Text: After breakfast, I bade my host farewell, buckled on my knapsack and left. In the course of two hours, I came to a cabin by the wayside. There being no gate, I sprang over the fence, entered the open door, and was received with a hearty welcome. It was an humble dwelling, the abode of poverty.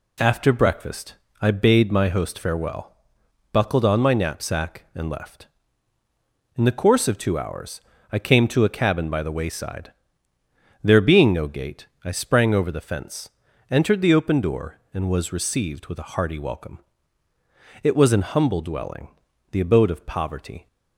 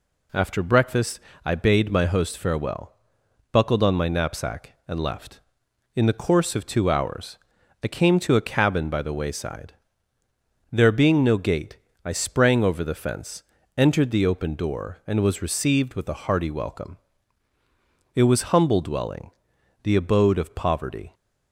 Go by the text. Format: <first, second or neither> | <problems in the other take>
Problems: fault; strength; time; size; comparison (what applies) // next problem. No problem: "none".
first | skips "an"; at 18.5 s